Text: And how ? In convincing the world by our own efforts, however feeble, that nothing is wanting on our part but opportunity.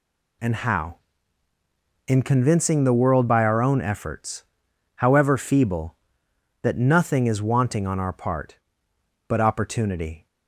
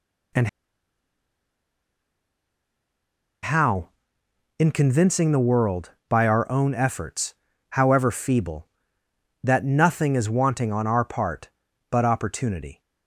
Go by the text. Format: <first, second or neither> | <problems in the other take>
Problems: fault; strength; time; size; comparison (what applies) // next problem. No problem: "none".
first | pauses between "And" and "how"; strong; at 0.4 s; 2.9 s long